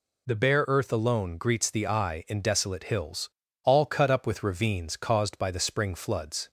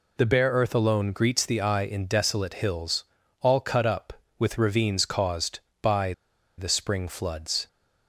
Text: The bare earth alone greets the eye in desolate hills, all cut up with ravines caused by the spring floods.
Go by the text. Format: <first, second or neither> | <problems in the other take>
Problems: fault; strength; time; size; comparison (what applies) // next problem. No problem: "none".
first | pauses between "by" and "the"; at 6.1 s; 0.45 s long